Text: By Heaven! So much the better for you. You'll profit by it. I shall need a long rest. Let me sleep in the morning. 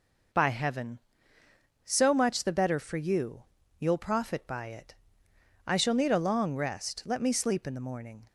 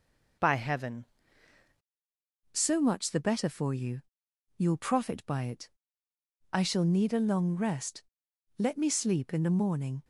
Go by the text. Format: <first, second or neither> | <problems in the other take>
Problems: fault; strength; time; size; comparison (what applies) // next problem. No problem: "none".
first | changes voice at "So"; from 2.5 s on; 7.5 s long